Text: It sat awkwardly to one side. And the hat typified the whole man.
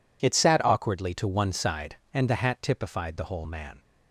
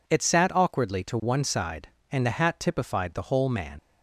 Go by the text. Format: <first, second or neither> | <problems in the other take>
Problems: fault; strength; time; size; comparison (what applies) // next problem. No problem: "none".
first | leaves "man" unfinished; at 3.7 s; 85 ms